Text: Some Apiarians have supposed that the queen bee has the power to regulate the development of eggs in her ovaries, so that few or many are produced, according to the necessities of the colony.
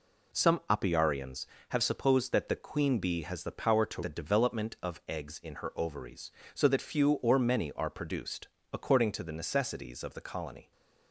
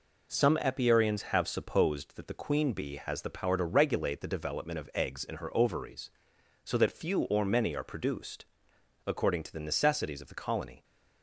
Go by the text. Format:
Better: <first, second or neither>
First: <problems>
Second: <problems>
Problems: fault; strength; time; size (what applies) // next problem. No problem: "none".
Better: second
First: skips "regulate"; at 4.0 s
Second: none